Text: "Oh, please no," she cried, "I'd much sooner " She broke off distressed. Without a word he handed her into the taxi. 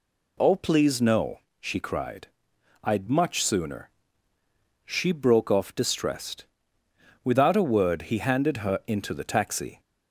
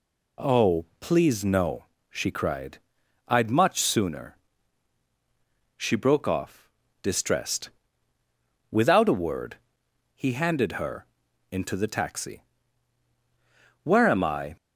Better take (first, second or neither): first